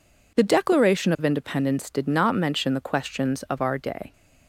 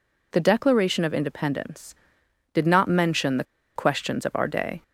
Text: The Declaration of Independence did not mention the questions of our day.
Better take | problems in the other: first | pauses between "the" and "questions"; slight; at 3.4 s; 0.30 s long

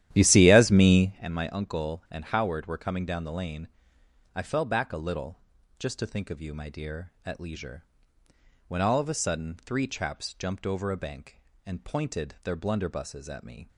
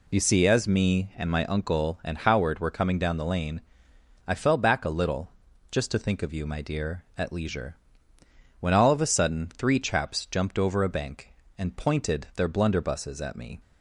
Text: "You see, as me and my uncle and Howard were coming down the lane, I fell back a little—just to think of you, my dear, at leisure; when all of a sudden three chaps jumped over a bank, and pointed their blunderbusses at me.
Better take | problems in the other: second | starts louder than the rest; strong; until 1.3 s; 12 dB

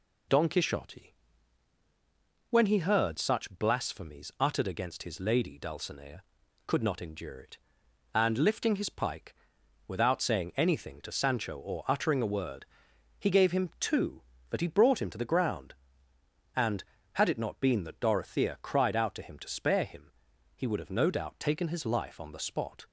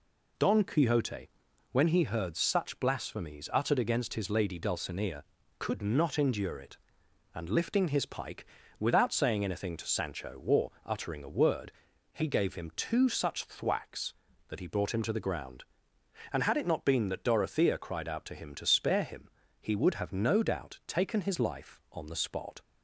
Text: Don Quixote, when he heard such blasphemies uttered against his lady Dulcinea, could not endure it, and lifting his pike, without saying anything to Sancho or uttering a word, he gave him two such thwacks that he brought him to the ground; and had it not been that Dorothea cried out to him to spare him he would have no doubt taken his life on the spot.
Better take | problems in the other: second | skips "such thwacks"; at 14.3 s // pauses between "him" and "he"; at 20.1 s; 0.42 s long; slight in the second

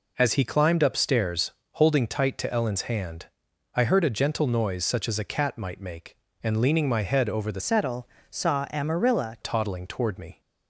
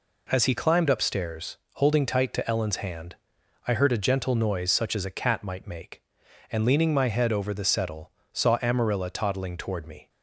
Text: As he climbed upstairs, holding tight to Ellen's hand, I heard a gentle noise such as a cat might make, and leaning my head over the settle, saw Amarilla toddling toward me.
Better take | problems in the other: second | changes voice from "settle" to "Amarilla"; from 7.5 to 9.3 s; 1.8 s long

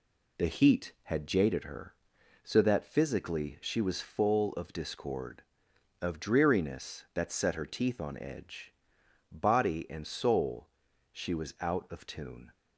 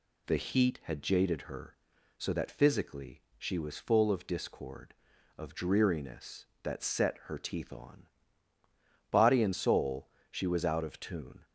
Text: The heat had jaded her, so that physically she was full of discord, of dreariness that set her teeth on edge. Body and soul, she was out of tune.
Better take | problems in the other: first | pauses between "physically" and "she"; slight; at 3.2 s; 0.16 s long // skips "edge"; at 8.5 s

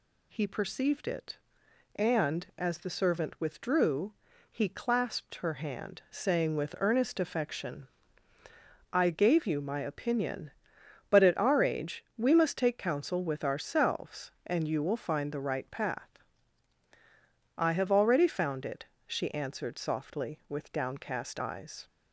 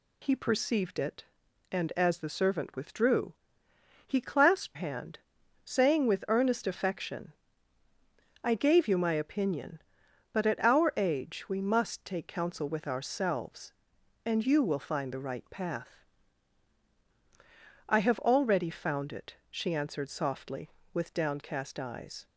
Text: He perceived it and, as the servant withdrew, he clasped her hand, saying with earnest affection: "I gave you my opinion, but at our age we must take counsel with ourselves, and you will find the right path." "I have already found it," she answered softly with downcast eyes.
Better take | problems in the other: first | skips "her"; at 4.7 s

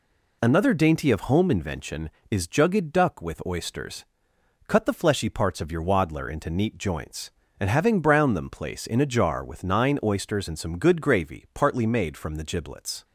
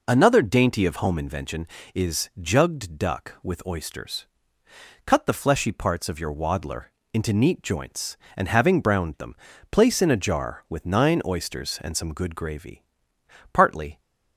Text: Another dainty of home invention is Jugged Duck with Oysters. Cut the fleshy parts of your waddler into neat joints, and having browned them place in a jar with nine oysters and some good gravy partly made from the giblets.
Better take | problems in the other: first | pauses between "waddler" and "into"; slight; at 6.8 s; 0.28 s long // pauses between "them" and "place"; slight; at 9.3 s; 0.34 s long // pauses between "gravy" and "partly"; noticeable; at 12.8 s; 0.68 s long // stops before "made from the giblets"; at 14.0 s

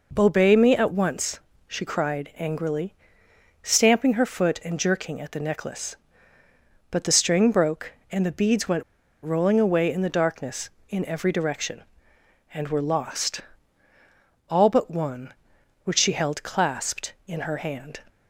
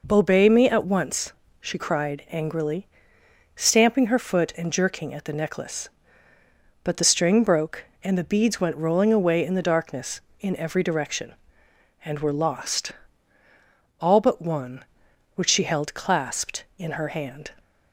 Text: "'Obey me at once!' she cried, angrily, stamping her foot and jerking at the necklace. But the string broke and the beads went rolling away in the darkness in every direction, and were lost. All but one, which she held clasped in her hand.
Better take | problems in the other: second | pauses between "went" and "rolling"; at 8.8 s; 0.39 s long

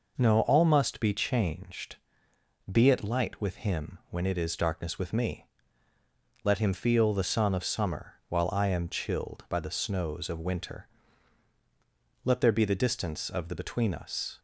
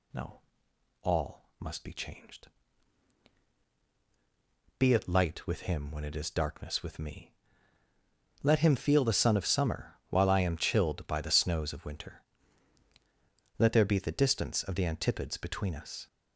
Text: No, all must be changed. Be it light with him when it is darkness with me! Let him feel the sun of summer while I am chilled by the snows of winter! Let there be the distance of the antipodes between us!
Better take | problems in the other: second | pauses between "summer" and "while"; slight; at 8.1 s; 0.16 s long; slight in the second // skips "antipodes"; at 13.5 s

